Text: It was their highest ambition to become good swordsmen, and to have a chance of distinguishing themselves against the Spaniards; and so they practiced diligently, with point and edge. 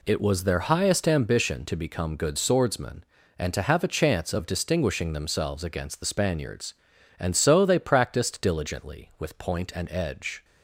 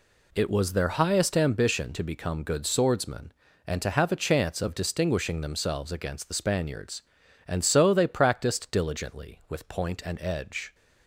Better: neither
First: none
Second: none

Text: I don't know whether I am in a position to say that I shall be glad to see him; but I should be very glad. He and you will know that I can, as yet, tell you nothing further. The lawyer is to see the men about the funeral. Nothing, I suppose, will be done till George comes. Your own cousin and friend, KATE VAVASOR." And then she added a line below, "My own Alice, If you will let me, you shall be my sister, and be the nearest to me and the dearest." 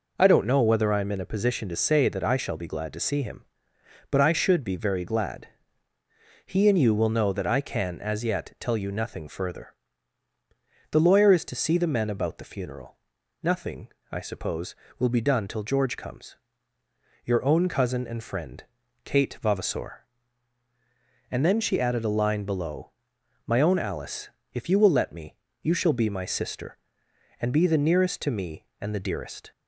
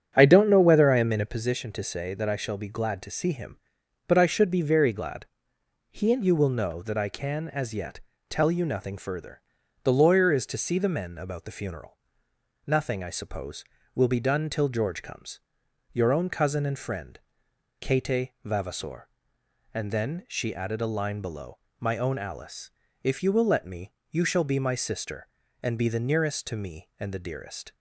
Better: first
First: none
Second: starts louder than the rest; strong; until 1.6 s; 9 dB // pauses between "KATE" and "VAVASOR"; slight; at 18.2 s; 0.16 s long

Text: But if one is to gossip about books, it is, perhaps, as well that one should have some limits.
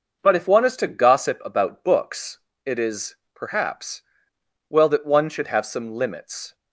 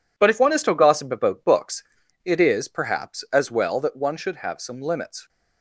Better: second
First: starts louder than the rest; noticeable; until 1.2 s; 6 dB // skips "as"; at 4.3 s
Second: none

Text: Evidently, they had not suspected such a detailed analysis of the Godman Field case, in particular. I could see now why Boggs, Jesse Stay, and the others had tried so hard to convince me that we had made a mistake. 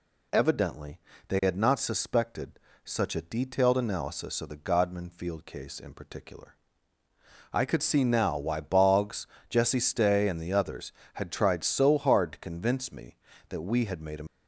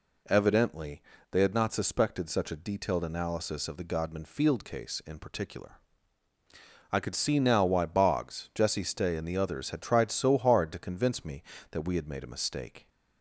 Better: second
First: pauses between "suspected" and "such"; slight; at 2.5 s; 0.24 s long // stops before "mistake"; at 14.2 s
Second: none

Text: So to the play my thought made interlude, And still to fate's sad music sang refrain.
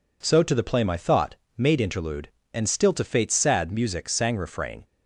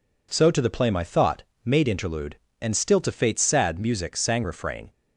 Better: neither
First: pauses between "thought" and "made"; slight; at 1.3 s; 0.22 s long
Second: pauses between "thought" and "made"; slight; at 1.4 s; 0.22 s long

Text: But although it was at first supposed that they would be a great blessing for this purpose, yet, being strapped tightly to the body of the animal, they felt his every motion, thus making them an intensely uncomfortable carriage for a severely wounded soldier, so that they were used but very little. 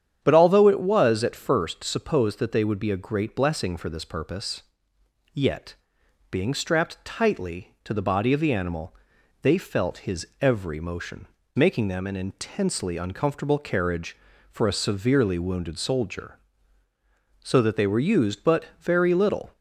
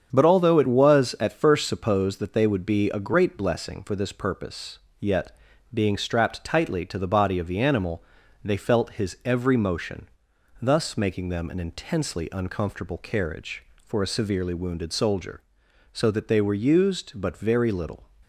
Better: second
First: starts louder than the rest; strong; until 1.2 s; 9 dB // skips "thus"; at 11.4 s // pauses between "but" and "very"; slight; at 18.6 s; 0.16 s long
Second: starts louder than the rest; strong; until 1.1 s; 7.5 dB

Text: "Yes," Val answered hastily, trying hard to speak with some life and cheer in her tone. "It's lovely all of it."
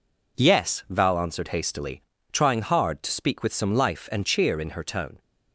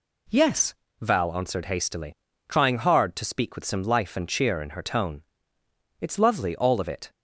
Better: second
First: stops before "It's lovely all of it"; at 5.1 s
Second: none

